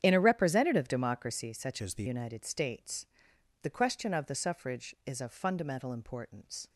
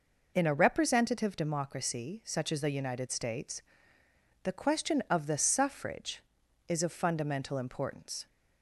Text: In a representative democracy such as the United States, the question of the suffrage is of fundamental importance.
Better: second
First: starts louder than the rest; strong; until 1.0 s; 9 dB // changes voice from "as" to "the"; from 1.8 to 2.0 s; 0.2 s long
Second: none

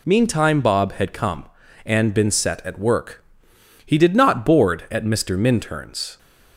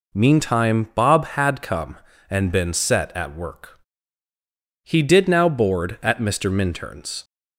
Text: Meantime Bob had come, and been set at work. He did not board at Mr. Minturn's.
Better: first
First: none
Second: says "now" for "not"; at 5.2 s

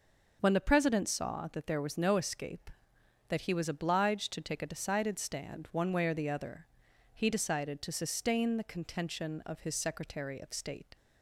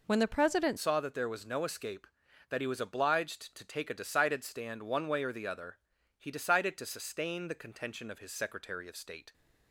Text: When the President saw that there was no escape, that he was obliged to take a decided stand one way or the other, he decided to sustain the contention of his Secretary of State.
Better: first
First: none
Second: changes voice at "saw"; from 0.7 s on; 8.6 s long

